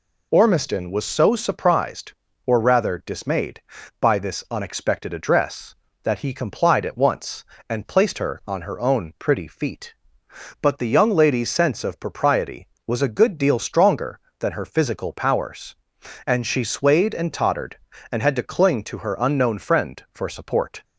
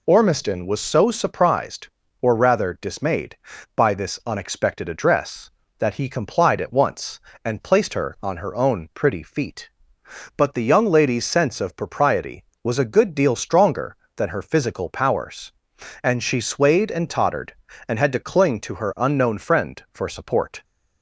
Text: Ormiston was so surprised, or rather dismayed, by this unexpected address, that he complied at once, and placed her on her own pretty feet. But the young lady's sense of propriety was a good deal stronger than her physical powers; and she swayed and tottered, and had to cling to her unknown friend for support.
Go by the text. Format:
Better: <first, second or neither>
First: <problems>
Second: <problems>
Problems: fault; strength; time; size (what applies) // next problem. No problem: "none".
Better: neither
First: none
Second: none